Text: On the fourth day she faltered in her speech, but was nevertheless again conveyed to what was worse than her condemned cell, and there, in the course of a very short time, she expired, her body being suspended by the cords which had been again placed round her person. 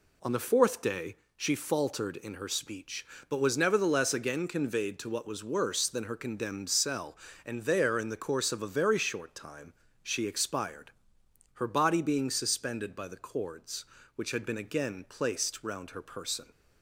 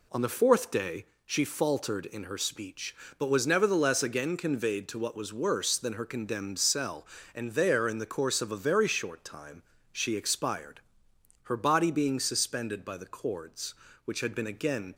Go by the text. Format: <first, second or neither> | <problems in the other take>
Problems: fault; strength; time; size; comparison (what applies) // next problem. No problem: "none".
first | pauses between "day" and "she"; slight; at 1.0 s; 0.22 s long; slight in the first // stops before "placed round her person"; at 14.9 s